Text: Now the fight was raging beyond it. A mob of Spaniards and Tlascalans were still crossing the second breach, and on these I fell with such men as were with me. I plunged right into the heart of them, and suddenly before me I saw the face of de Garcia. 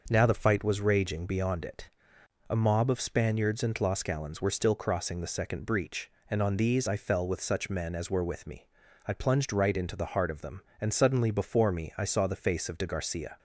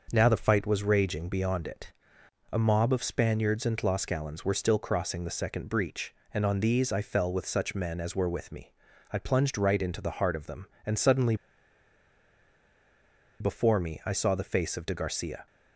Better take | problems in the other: first | starts louder than the rest; noticeable; until 1.1 s; 6 dB // pauses between "suddenly" and "before"; strong; at 11.3 s; 2.0 s long

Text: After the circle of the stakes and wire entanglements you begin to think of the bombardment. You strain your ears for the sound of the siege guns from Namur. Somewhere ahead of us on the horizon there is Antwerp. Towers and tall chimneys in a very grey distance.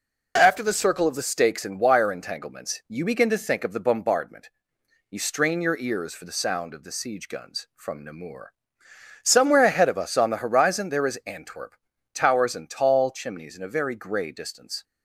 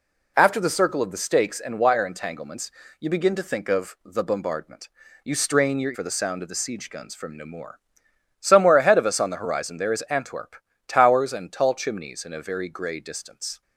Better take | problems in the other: first | pauses between "entanglements" and "you"; slight; at 2.6 s; 0.30 s long // skips "ears"; at 5.9 s

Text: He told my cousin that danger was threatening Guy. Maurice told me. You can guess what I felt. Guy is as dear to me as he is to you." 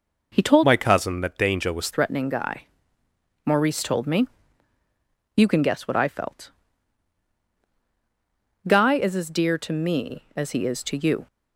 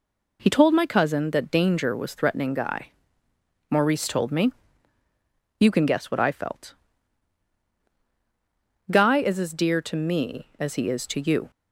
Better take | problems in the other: second | changes voice from "my" to "was"; from 0.6 to 1.8 s; 1.2 s long

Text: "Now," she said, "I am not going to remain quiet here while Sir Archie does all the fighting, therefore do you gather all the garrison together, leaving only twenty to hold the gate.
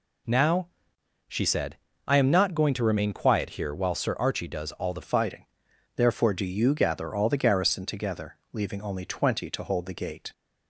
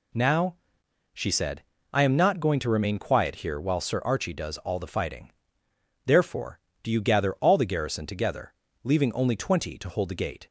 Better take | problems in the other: second | changes voice at "fighting"; from 5.0 s on; 5.3 s long

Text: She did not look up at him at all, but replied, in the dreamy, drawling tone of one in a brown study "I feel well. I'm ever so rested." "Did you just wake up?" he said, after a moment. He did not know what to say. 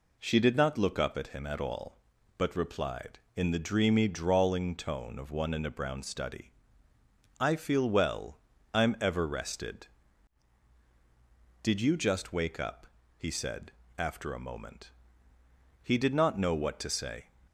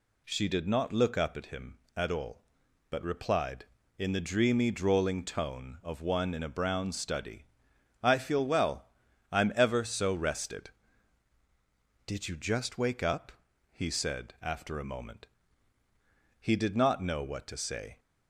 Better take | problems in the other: second | pauses between "study" and "I"; noticeable; at 6.5 s; 0.88 s long; noticeable in the second // skips "so"; at 9.2 s

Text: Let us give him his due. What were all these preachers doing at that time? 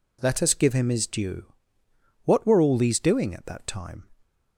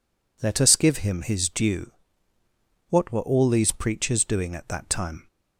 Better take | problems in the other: second | skips "preachers"; at 2.9 s

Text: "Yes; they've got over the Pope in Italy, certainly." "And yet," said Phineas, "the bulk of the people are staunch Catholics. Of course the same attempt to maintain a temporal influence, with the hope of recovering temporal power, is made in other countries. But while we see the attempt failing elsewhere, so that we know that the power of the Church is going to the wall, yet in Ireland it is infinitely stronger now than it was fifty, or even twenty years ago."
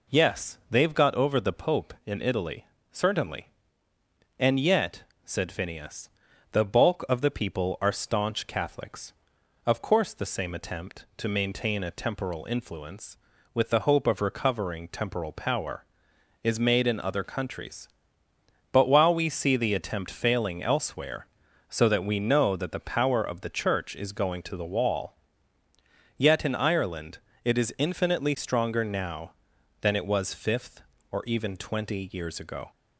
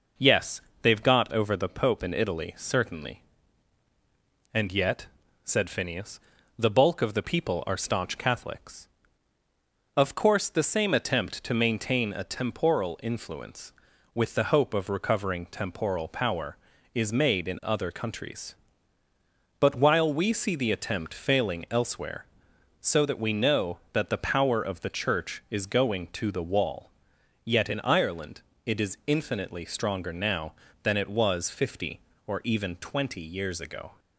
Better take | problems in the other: second | pauses between "Ireland" and "it"; slight; at 27.1 s; 0.26 s long; slight in the second // says "fifth" for "fifty"; at 30.3 s

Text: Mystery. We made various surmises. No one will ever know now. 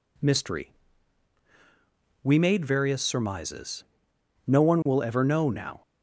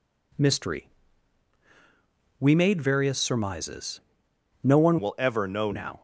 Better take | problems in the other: first | changes voice from "will" to "know"; from 4.9 to 5.6 s; 0.7 s long

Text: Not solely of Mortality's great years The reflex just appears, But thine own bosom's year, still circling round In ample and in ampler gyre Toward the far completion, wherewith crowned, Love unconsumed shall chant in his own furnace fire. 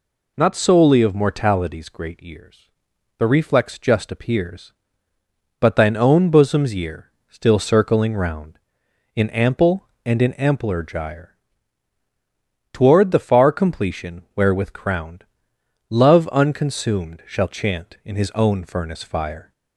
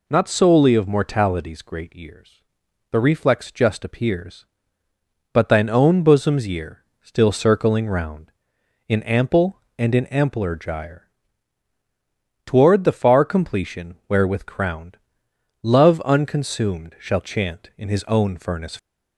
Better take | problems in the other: first | pauses between "years" and "The"; noticeable; at 2.4 s; 0.48 s long; noticeable in the first // pauses between "gyre" and "Toward"; strong; at 11.0 s; 1.3 s long; strong in the first // stops before "fire"; at 18.7 s

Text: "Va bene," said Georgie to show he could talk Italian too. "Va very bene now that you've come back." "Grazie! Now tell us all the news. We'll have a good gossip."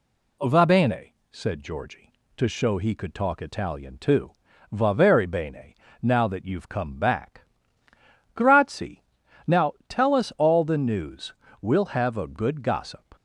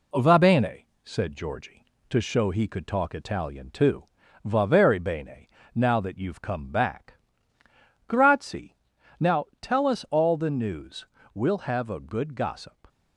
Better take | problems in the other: first | gets quieter; slight; throughout; 3 dB // pauses between "bene" and "now"; slight; at 5.4 s; 0.26 s long; slight in the first // pauses between "Now" and "tell"; slight; at 9.4 s; 0.16 s long; slight in the first

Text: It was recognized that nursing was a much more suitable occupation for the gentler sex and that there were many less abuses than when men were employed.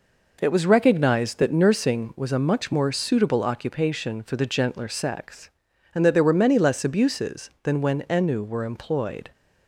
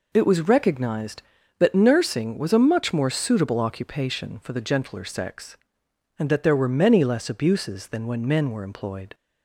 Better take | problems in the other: second | says "ennu" for "men"; at 8.0 s

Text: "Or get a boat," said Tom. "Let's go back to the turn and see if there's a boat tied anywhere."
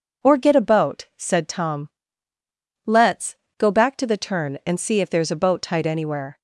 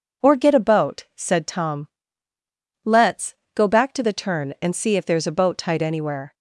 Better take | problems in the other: neither | pauses between "Let's" and "go"; slight; the same in both

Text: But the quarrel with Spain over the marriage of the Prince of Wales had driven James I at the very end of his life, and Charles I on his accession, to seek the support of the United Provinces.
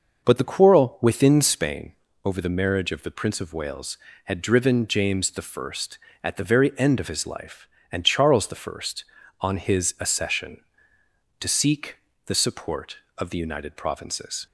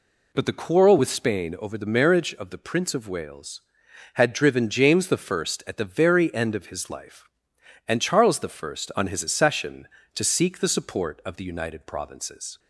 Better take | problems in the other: second | says "within" for "with"; at 1.0 s // pauses between "Spain" and "over"; slight; at 1.9 s; 0.32 s long // pauses between "seek" and "the"; slight; at 11.9 s; 0.30 s long

